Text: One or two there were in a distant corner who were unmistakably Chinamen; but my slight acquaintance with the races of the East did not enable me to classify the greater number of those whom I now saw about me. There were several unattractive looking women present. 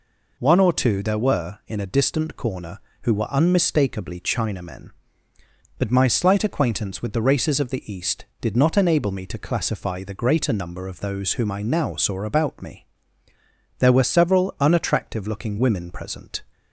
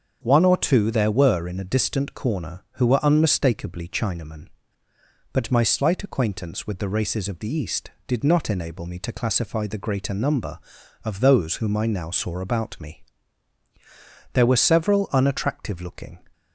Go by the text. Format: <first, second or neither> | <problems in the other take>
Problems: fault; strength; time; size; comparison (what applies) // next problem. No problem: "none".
first | starts louder than the rest; until 1.2 s; 7 dB // stops before "women present"; at 16.3 s